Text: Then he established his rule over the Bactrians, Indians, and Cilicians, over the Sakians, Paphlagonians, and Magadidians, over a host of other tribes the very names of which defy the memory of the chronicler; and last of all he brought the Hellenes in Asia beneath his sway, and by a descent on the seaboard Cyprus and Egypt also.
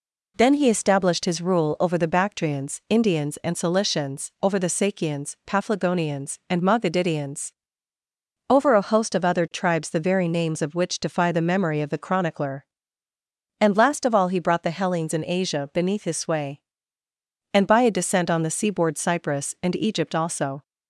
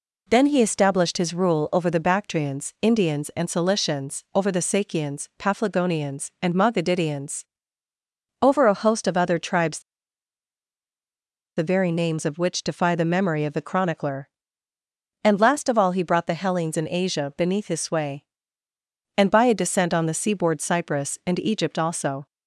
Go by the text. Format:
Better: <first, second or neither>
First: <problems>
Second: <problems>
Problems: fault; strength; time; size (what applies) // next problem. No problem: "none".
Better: first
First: none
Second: pauses between "tribes" and "the"; strong; at 9.7 s; 1.7 s long